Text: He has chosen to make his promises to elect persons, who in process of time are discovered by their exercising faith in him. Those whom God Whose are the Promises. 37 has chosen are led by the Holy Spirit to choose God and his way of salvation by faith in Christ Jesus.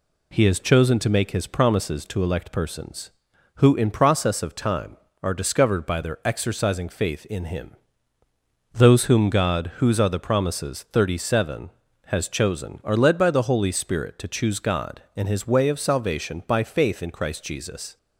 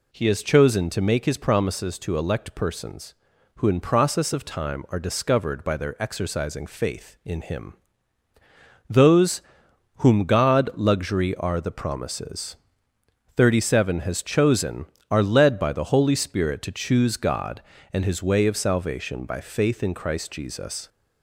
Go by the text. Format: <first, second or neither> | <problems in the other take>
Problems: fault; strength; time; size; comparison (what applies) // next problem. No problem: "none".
first | pauses between "Those" and "whom"; noticeable; at 9.4 s; 0.56 s long // says "Luxury" for "Whose"; at 10.7 s